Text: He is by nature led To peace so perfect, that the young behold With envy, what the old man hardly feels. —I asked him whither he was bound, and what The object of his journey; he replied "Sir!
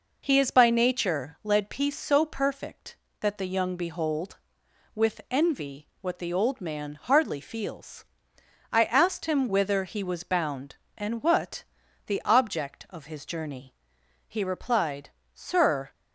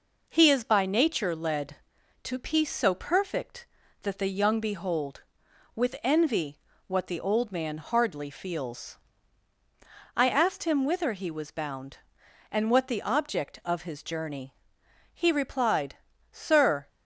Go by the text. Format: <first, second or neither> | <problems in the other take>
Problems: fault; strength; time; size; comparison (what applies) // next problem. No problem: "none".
second | skips "To"; at 1.6 s // pauses between "what" and "The"; at 11.6 s; 0.42 s long // pauses between "replied" and "Sir"; slight; at 15.0 s; 0.24 s long; slight in the second